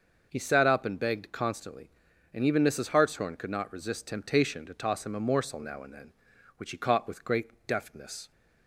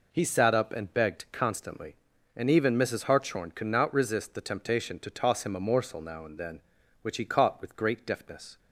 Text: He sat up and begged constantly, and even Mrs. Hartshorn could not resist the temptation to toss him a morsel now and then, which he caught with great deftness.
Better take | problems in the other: second | starts louder than the rest; until 1.3 s; 6 dB // skips "the"; at 4.0 s

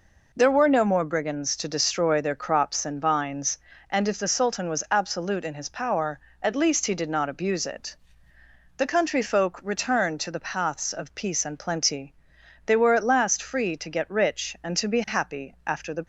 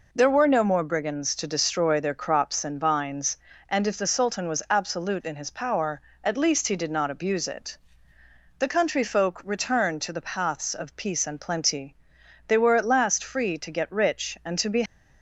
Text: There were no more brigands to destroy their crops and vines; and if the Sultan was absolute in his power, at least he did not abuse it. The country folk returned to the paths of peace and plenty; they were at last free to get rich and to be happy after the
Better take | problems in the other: first | stops before "happy after the"; at 14.8 s

